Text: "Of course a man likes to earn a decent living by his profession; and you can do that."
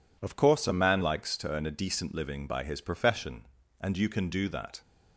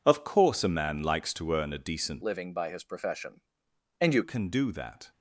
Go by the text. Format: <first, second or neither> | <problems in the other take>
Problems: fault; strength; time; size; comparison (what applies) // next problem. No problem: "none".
first | changes voice from "living" to "you"; from 2.2 to 4.2 s; 2.0 s long